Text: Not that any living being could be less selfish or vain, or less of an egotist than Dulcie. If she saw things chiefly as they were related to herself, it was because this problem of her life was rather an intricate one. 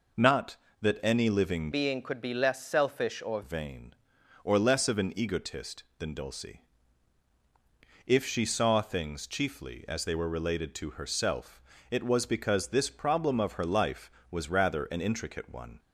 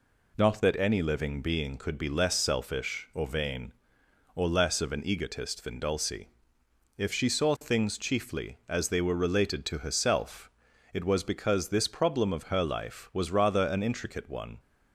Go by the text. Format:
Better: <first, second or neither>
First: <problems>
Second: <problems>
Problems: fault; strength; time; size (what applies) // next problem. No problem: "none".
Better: second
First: changes voice from "being" to "or"; from 1.7 to 3.4 s; 1.7 s long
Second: none